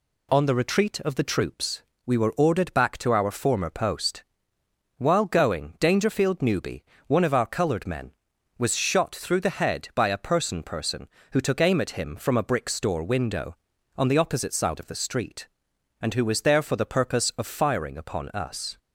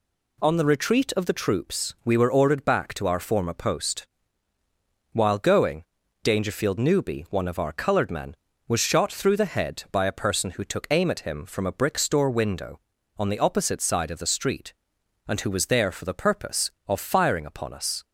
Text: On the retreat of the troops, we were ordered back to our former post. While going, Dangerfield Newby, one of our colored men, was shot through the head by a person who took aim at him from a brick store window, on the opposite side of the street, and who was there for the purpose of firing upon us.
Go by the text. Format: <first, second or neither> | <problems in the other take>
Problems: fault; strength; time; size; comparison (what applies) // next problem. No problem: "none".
second | says "person" twice; at 10.6 s